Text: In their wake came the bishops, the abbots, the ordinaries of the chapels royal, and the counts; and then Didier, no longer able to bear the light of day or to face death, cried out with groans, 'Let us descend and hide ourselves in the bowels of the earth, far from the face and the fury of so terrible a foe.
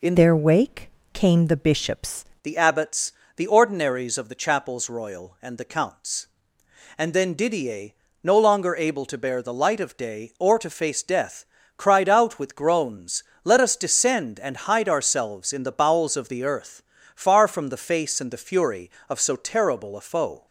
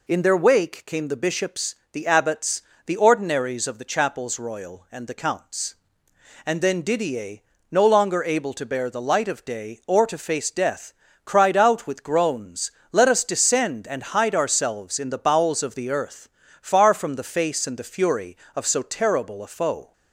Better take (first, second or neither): second